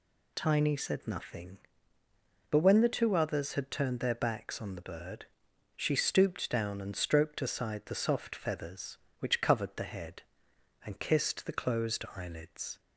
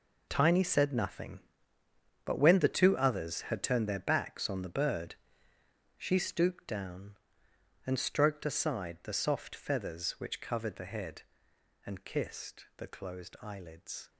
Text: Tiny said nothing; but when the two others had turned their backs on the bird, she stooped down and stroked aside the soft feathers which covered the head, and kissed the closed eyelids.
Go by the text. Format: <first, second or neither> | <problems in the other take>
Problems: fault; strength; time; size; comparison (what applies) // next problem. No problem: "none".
first | gets quieter; strong; throughout; 13 dB